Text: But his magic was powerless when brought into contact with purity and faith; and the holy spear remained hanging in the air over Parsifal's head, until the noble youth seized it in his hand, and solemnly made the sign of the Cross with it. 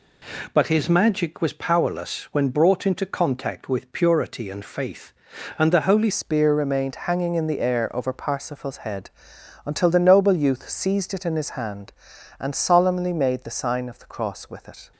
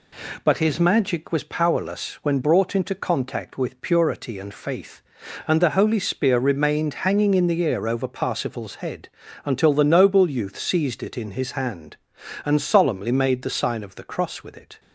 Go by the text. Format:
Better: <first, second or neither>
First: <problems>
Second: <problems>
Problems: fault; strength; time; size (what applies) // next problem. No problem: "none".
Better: second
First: changes voice at "spear"; from 6.1 s on; 8.8 s long // pauses between "remained" and "hanging"; slight; at 6.9 s; 0.16 s long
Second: none